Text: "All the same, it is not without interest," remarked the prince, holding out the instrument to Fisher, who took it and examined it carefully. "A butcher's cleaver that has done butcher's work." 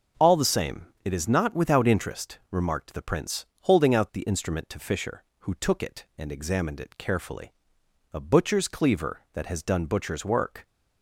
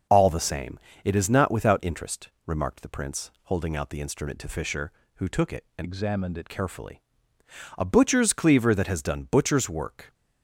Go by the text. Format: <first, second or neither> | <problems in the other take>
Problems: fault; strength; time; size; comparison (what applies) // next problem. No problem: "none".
first | changes voice from "examined" to "it"; from 5.8 to 6.5 s; 0.7 s long